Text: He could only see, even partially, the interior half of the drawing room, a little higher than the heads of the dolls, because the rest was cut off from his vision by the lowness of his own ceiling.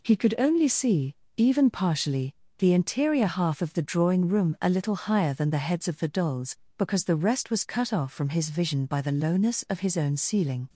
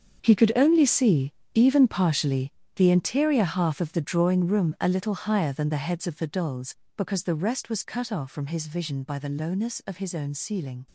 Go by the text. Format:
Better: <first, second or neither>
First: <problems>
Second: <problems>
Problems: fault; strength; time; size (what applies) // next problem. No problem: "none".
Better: first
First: none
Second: gets quieter; strong; throughout; 12.5 dB